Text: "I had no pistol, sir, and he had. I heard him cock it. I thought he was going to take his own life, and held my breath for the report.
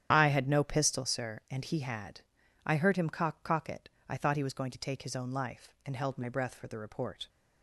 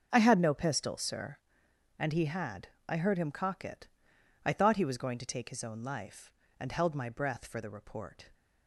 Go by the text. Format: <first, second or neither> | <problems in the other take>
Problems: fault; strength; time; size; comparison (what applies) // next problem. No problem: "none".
second | starts louder than the rest; strong; until 1.1 s; 10 dB; also in the second // says "cock" twice; at 3.4 s